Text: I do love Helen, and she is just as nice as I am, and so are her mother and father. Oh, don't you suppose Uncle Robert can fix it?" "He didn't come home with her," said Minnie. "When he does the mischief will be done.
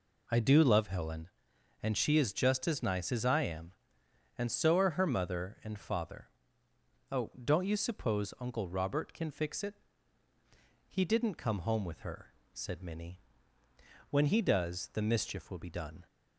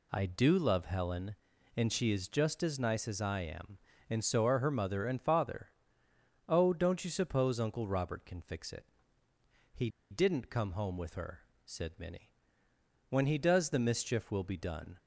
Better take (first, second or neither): first